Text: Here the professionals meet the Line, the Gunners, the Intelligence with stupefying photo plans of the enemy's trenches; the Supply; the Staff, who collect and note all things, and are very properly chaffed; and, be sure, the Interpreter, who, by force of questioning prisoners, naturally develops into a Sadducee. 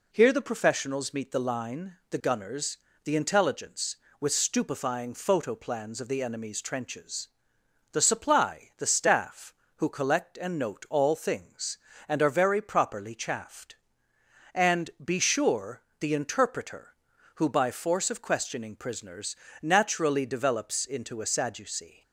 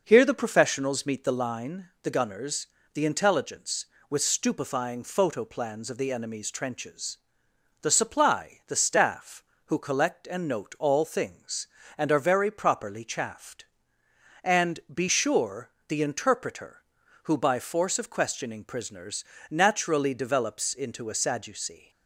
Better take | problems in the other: first | starts louder than the rest; noticeable; until 1.4 s; 5.5 dB

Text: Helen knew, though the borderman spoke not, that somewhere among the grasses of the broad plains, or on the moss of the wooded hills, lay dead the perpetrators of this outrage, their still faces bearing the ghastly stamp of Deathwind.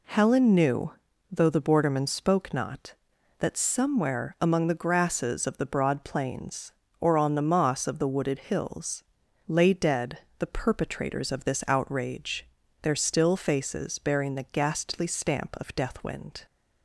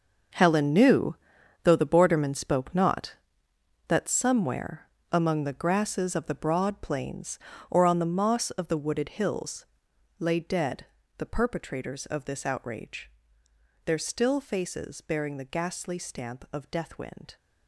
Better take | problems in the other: first | gets quieter; strong; throughout; 13.5 dB // pauses between "somewhere" and "among"; slight; at 4.8 s; 0.22 s long // pauses between "dead" and "the"; slight; at 10.8 s; 0.32 s long; slight in the first

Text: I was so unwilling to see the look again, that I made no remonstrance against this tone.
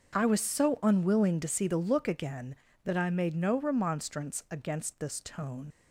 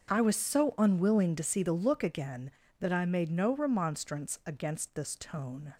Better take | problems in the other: second | starts louder than the rest; until 1.2 s; 6.5 dB; also in the second // leaves "tone" unfinished; at 5.7 s; 100 ms

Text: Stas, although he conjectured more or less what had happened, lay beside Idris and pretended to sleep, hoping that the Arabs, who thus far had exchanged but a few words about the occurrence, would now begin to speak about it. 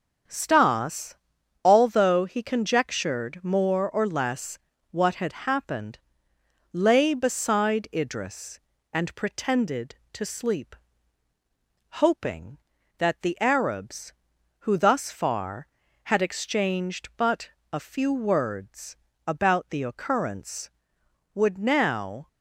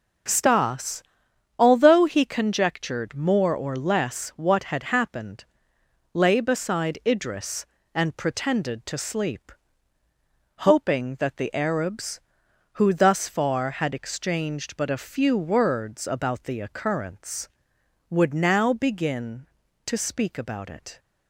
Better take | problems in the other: second | starts louder than the rest; strong; until 1.7 s; 7 dB // pauses between "less" and "what"; slight; at 4.5 s; 0.34 s long // pauses between "but" and "a"; slight; at 17.4 s; 0.22 s long // pauses between "words" and "about"; slight; at 18.9 s; 0.32 s long // stops before "begin to speak about it"; at 22.2 s

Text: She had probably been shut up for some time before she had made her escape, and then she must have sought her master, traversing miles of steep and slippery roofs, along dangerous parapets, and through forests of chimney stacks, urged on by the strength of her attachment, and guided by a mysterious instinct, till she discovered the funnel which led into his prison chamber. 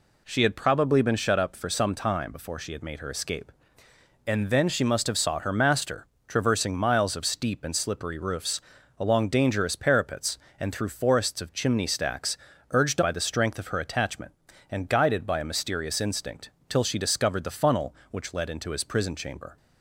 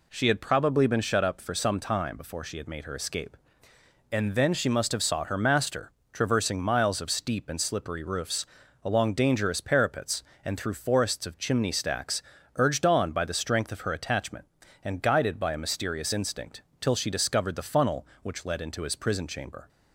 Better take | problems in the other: second | skips "on"; at 13.0 s

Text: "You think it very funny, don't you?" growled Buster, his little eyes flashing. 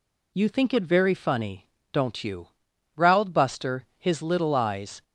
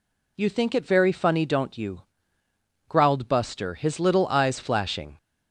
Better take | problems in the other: second | stops before "flashing"; at 5.0 s

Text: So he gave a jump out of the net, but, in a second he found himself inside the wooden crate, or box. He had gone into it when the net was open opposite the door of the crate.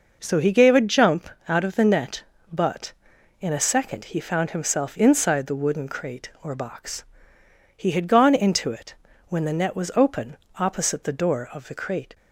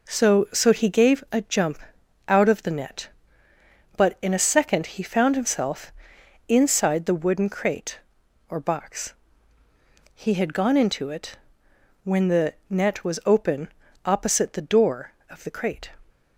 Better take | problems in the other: first | says "So" twice; at 0.5 s // pauses between "jump" and "out"; noticeable; at 1.7 s; 0.50 s long; slight in the first // pauses between "himself" and "inside"; noticeable; at 5.9 s; 0.56 s long // pauses between "it" and "when"; noticeable; at 11.3 s; 0.66 s long; slight in the first // pauses between "the" and "net"; slight; at 12.5 s; 0.16 s long // pauses between "open" and "opposite"; at 13.6 s; 0.38 s long; slight in the first

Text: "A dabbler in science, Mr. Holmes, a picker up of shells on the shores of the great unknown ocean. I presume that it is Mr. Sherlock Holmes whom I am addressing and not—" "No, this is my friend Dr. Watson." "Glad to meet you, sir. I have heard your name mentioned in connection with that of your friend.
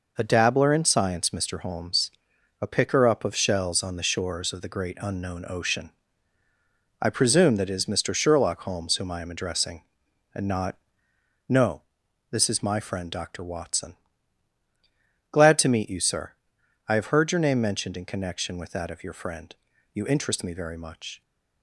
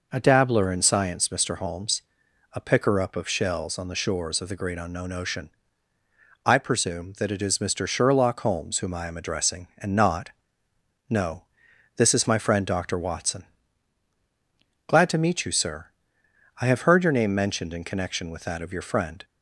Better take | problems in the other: second | goes on to say "You interest me very much"; noticeable; from 19.9 s on; 1.2 s long

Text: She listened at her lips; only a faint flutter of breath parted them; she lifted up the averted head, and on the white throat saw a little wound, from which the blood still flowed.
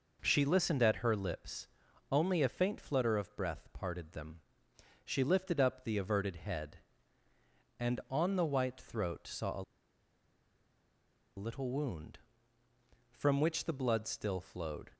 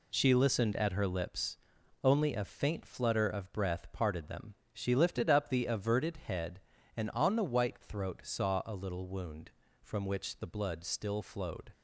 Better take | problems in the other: second | pauses between "a" and "little"; strong; at 9.6 s; 1.7 s long

